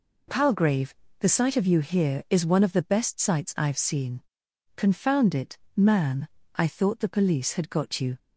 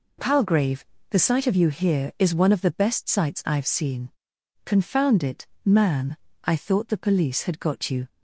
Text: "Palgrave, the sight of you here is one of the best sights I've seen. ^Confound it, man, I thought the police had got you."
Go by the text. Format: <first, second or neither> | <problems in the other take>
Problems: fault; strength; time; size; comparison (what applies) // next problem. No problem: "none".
neither | none